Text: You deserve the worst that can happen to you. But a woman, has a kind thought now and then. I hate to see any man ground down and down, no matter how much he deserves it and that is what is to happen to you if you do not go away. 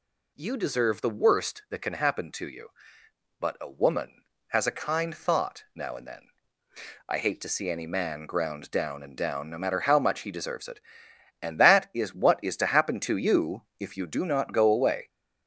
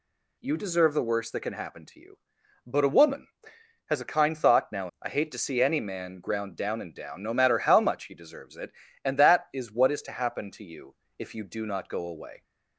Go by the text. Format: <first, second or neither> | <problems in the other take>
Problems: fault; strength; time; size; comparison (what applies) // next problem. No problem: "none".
first | skips "and then"; at 4.9 s // pauses between "you" and "if"; slight; at 10.9 s; 0.22 s long; slight in the first